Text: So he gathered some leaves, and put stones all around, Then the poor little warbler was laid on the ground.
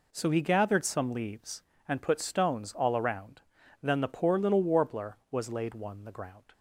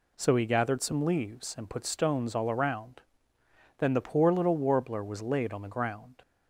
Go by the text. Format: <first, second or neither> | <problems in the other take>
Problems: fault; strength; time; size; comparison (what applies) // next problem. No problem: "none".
second | says "one" for "on"; at 5.7 s